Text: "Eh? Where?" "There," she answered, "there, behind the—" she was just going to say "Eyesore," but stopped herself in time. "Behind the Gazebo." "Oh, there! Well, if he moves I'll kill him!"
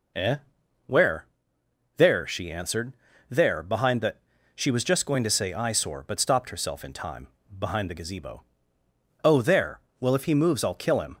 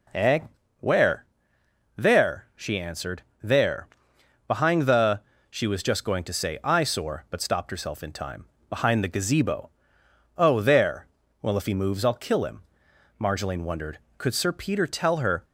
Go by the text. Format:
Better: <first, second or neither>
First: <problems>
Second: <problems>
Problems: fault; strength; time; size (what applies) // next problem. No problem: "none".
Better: first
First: none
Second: goes on to say "Marjolaine wondered Could Sir Peter tell her"; strong; from 13.2 s on; 2.2 s long